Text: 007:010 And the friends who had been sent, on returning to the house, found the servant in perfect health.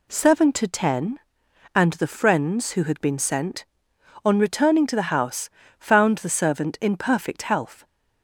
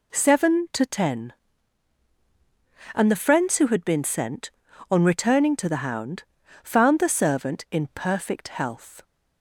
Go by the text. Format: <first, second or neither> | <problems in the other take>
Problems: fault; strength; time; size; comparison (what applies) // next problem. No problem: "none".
first | says "hound" for "house"; at 5.8 s